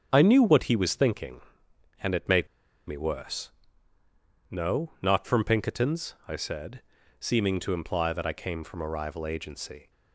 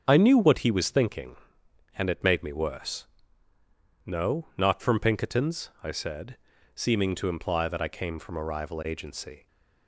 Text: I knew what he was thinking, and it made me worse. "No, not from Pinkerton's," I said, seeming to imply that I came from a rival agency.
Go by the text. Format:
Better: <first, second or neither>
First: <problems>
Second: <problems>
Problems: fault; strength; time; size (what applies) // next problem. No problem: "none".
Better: second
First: starts louder than the rest; strong; until 1.1 s; 7.5 dB // pauses between "made" and "me"; at 2.4 s; 0.41 s long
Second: starts louder than the rest; strong; until 1.0 s; 7.5 dB